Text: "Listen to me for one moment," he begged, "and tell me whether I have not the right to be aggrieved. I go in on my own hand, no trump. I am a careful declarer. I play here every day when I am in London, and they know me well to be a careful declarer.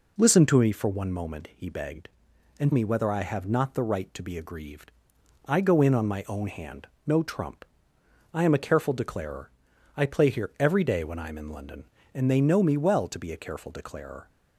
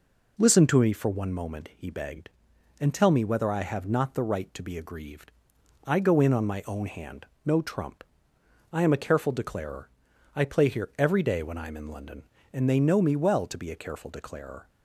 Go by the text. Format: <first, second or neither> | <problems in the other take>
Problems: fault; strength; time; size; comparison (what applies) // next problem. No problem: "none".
second | skips "tell"; at 2.7 s